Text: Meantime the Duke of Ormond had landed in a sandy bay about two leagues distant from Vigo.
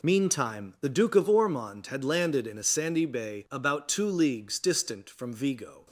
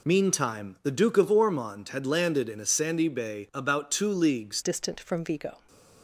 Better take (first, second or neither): first